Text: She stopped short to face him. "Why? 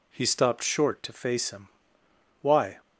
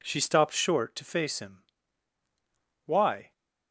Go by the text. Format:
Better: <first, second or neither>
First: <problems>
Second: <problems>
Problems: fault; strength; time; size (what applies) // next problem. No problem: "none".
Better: second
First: says "He" for "She"; at 0.1 s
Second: none